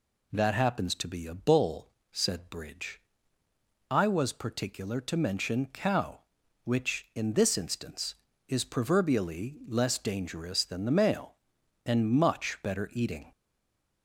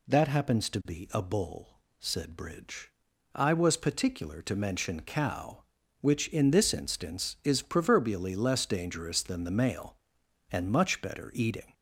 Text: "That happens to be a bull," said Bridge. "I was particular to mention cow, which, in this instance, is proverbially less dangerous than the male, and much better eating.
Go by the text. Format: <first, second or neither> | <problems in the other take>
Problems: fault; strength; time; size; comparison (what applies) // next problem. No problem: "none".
second | stays silent after the last word; slight; from 13.3 s on; 0.7 s long